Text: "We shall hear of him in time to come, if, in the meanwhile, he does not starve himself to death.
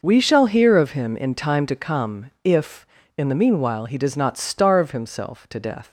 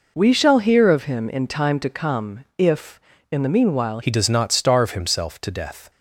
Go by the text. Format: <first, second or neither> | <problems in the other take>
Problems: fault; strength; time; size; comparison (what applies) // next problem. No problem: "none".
first | changes voice at "he"; from 4.0 s on; 1.9 s long